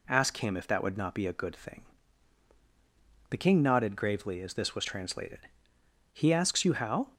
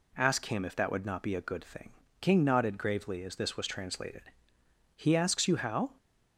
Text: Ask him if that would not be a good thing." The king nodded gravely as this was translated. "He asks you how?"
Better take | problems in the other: first | skips "The"; at 2.0 s

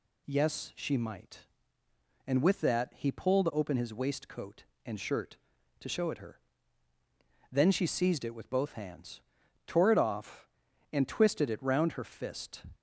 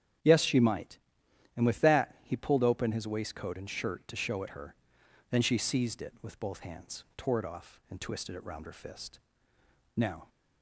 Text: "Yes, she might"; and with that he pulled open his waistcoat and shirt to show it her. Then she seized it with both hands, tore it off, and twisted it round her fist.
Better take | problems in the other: first | starts louder than the rest; strong; until 1.8 s; 9 dB // goes on to say "Now"; slight; from 9.9 s on; 0.34 s long

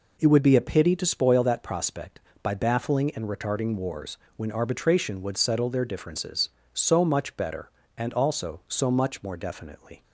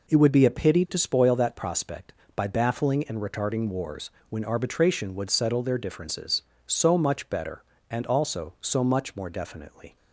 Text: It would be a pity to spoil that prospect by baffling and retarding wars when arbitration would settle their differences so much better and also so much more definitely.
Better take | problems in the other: neither | pauses between "wars" and "when"; slight; the same in both

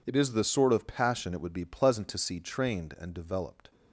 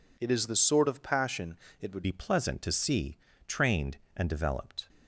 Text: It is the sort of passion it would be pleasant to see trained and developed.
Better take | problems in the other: first | pauses between "passion" and "it"; slight; at 1.5 s; 0.24 s long // changes voice at "be"; from 2.0 s on; 2.8 s long // pauses between "see" and "trained"; slight; at 3.1 s; 0.32 s long

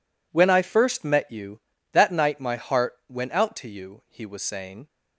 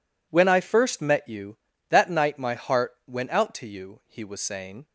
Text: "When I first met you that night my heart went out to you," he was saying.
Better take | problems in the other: neither | pauses between "heart" and "went"; slight; the same in both

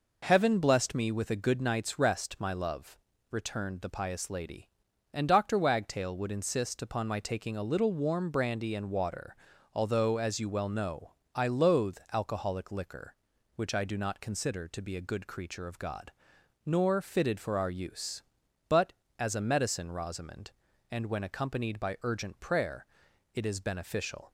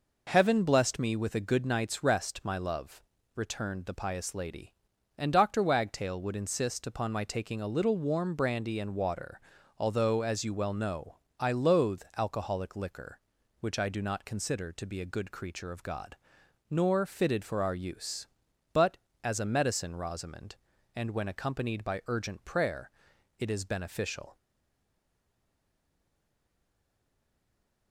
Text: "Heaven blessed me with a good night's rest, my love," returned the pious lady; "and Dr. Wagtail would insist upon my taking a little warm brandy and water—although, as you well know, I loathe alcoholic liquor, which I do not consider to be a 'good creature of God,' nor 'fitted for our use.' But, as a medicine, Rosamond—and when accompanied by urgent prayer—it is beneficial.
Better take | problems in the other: first | pauses between "loathe" and "alcoholic"; slight; at 12.0 s; 0.16 s long; slight in the first // stays silent after the last word; strong; from 24.3 s on; 3.6 s long

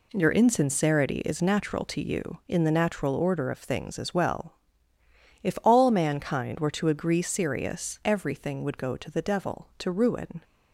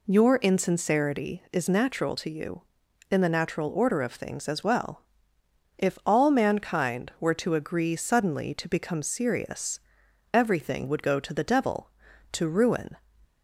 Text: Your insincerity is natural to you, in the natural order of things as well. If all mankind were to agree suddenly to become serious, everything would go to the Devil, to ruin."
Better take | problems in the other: second | skips "suddenly to become"; at 7.1 s

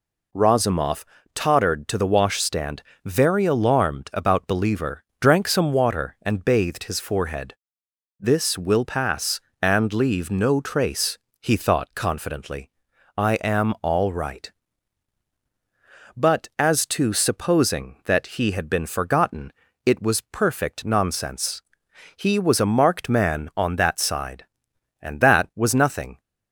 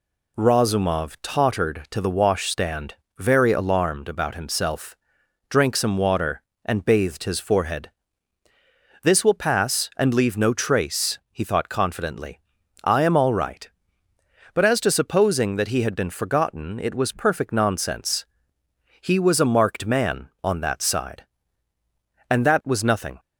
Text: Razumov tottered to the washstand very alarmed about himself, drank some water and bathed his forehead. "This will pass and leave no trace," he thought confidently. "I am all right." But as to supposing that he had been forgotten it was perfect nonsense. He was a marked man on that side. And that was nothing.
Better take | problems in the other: second | pauses between "Razumov" and "tottered"; slight; at 1.0 s; 0.30 s long // pauses between "washstand" and "very"; slight; at 2.8 s; 0.24 s long; slight in the second // says "believer" for "himself"; at 4.4 s // pauses between "forgotten" and "it"; slight; at 19.5 s; 0.34 s long

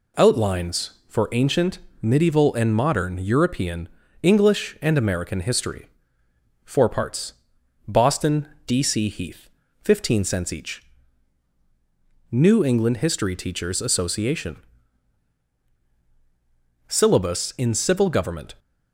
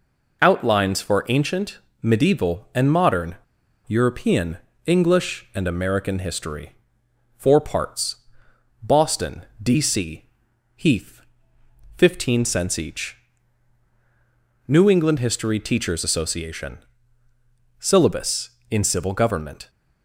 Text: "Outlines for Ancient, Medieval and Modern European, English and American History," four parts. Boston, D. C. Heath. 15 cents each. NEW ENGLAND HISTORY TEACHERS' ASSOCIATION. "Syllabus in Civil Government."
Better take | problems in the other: first | pauses between "Modern" and "European"; noticeable; at 3.3 s; 0.51 s long // pauses between "C" and "Heath"; noticeable; at 10.2 s; 0.50 s long

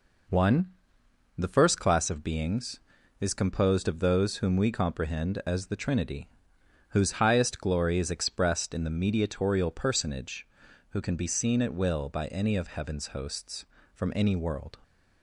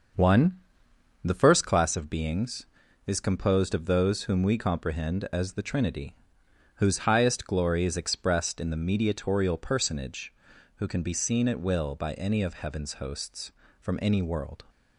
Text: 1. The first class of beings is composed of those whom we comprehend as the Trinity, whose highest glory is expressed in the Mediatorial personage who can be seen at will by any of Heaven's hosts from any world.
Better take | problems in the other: first | starts louder than the rest; until 1.8 s; 6 dB

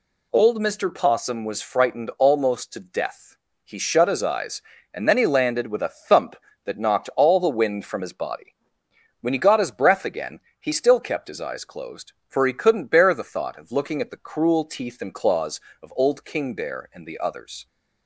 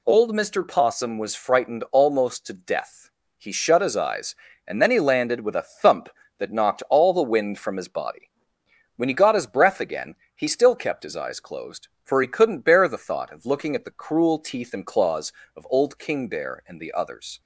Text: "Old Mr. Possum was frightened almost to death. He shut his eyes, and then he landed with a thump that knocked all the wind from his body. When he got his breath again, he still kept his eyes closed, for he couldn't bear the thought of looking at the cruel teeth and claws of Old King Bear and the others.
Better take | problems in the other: neither | none

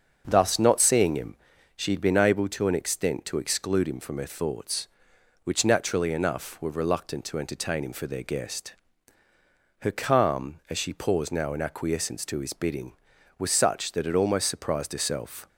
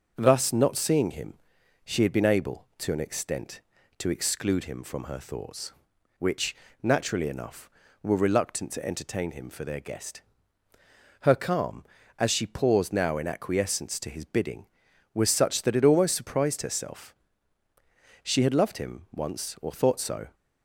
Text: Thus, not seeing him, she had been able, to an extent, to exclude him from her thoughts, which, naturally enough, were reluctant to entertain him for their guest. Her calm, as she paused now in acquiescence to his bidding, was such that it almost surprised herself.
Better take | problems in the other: first | starts louder than the rest; until 1.1 s; 6.5 dB; also in the first // goes on to say "She had loved him once or thought so"; strong; from 18.2 s on; 2.1 s long

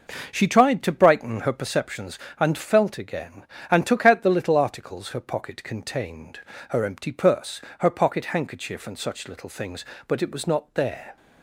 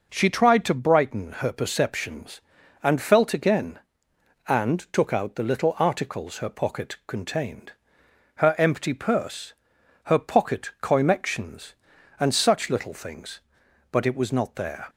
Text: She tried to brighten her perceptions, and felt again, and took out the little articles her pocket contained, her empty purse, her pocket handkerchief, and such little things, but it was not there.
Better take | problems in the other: first | says "coimections" for "handkerchief"; at 10.8 s

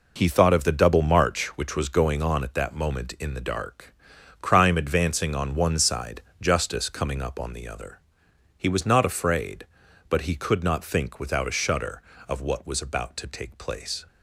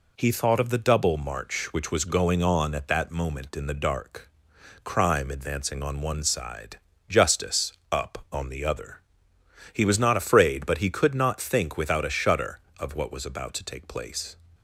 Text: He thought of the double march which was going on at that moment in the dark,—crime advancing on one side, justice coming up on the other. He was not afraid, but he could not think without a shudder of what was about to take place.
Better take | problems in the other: first | skips "coming"; at 7.8 s

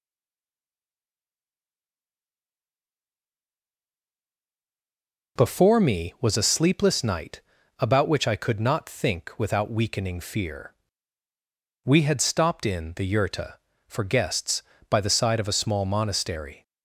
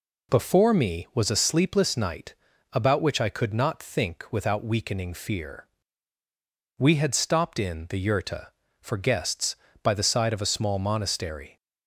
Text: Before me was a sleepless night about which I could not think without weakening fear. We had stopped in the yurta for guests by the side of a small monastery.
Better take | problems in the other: second | stays silent before the first word; strong; until 5.3 s; 5.3 s long // pauses between "night" and "about"; at 7.4 s; 0.38 s long; also in the second

